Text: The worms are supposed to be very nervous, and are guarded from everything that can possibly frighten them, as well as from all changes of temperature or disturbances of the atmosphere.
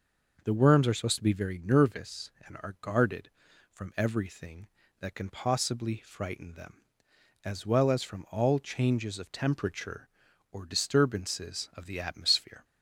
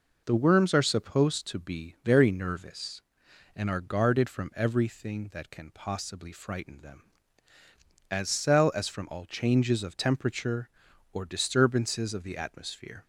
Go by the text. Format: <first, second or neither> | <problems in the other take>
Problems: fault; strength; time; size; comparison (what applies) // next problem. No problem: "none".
first | says "cell" for "well"; at 8.2 s